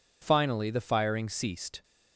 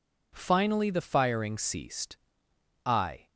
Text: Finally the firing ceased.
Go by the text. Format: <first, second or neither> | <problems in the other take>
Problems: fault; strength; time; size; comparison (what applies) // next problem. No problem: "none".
first | goes on to say "I"; slight; from 2.8 s on; 0.44 s long